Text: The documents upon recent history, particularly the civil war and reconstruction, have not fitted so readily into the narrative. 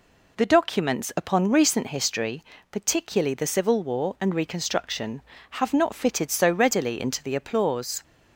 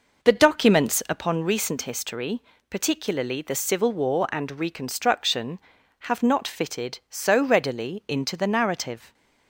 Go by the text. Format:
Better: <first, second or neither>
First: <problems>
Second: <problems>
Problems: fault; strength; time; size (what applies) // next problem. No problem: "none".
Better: second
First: says "applause" for "narrative"; at 7.3 s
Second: none